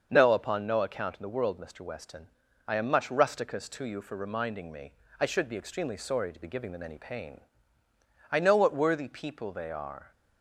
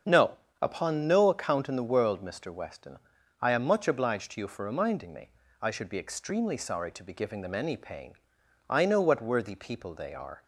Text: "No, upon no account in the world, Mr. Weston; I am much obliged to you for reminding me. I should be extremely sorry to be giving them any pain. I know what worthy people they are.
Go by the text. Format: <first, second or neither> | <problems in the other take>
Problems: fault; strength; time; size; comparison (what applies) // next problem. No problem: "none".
second | starts louder than the rest; until 1.1 s; 6.5 dB; strong in the second // says "rusticus" for "obliged"; at 3.0 s